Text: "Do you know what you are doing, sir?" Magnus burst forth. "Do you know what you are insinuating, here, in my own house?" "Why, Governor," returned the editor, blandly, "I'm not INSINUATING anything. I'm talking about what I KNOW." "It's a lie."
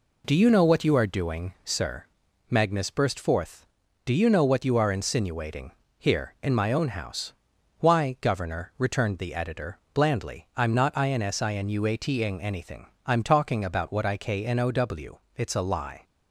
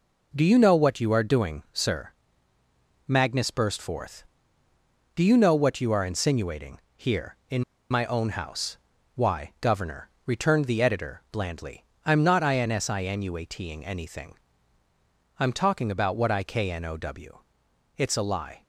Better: first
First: none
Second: pauses between "in" and "my"; slight; at 7.6 s; 0.28 s long

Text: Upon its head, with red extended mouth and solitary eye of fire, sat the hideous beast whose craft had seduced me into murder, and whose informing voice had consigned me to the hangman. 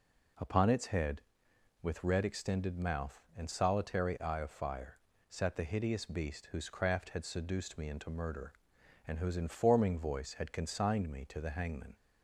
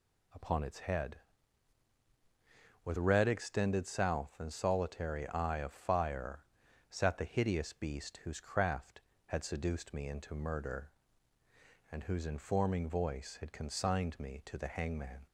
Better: first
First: none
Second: says "south" for "mouth"; at 3.8 s

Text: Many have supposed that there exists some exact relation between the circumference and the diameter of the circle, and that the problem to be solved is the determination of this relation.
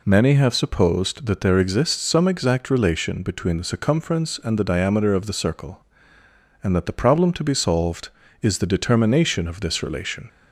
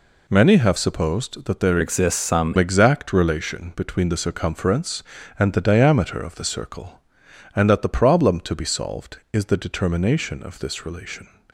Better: first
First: none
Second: changes voice from "exists" to "some"; from 1.8 to 2.5 s; 0.7 s long

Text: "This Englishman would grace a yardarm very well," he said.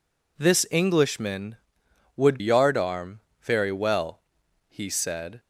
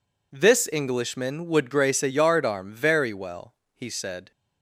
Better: second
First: skips "grace a"; at 2.3 s // pauses between "yardarm" and "very"; slight; at 3.1 s; 0.20 s long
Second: none

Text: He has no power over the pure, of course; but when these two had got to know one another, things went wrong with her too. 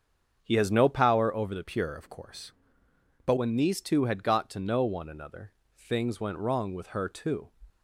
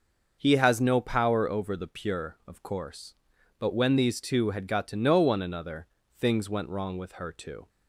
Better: second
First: starts louder than the rest; strong; until 1.4 s; 7.5 dB // changes voice from "pure" to "but"; from 1.6 to 3.3 s; 1.7 s long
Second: starts louder than the rest; until 1.4 s; 6.5 dB

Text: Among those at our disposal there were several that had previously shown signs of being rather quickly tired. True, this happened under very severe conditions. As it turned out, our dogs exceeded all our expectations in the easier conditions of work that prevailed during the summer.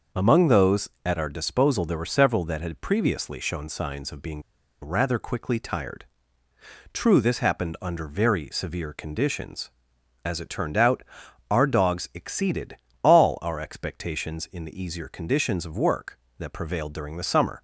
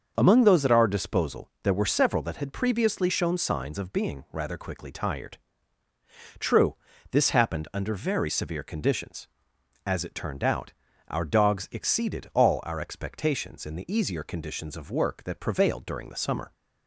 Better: second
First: starts louder than the rest; noticeable; until 1.3 s; 6 dB // pauses between "being" and "rather"; at 4.4 s; 0.41 s long // pauses between "exceeded" and "all"; slight; at 12.7 s; 0.26 s long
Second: starts louder than the rest; until 1.1 s; 6.5 dB

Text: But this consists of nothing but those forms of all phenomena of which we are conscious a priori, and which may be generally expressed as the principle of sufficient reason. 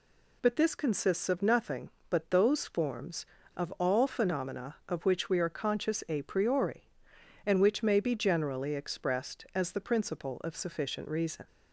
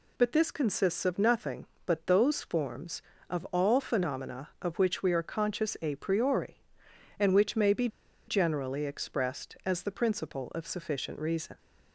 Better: first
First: none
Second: pauses between "be" and "generally"; at 7.8 s; 0.40 s long

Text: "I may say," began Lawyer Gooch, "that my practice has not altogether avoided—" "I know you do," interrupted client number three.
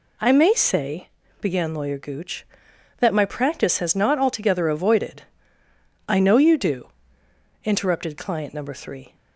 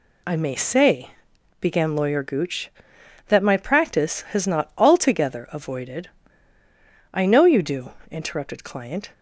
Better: first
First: none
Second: stops before "number three"; at 9.1 s

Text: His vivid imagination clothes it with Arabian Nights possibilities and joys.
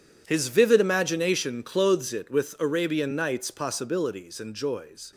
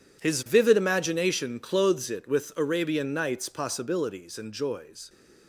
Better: neither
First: none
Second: none

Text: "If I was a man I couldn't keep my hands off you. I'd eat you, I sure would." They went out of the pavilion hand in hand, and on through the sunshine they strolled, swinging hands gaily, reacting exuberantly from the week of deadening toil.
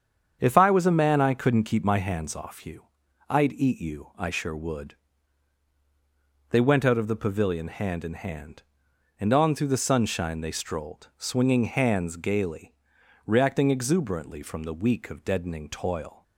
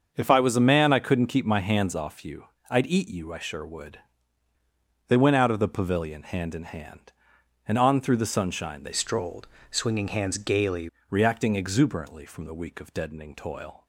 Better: first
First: starts louder than the rest; strong; until 1.4 s; 7.5 dB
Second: starts louder than the rest; until 1.1 s; 6.5 dB // changes voice from "strolled" to "gaily"; from 8.9 to 10.8 s; 1.9 s long

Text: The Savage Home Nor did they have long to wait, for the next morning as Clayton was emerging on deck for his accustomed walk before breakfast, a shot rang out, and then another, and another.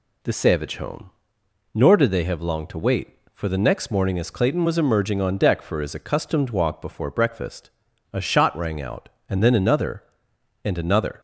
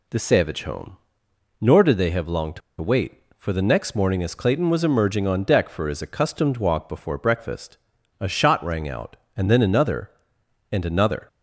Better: first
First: pauses between "Home" and "Nor"; noticeable; at 1.1 s; 0.62 s long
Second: pauses between "Home" and "Nor"; noticeable; at 0.9 s; 0.62 s long // pauses between "to" and "wait"; slight; at 2.6 s; 0.20 s long

